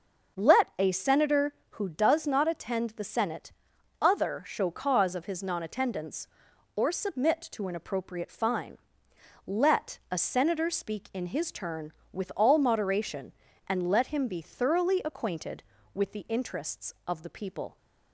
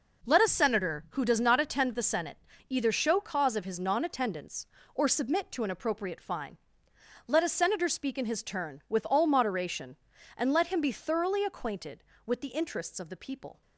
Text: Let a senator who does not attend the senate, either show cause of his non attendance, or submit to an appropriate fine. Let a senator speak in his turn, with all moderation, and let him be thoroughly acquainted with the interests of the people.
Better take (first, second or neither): second